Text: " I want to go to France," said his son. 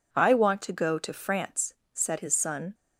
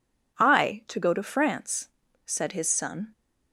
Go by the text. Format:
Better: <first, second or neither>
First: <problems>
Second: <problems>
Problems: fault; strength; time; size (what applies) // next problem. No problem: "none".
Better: first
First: none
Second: skips "want"; at 0.8 s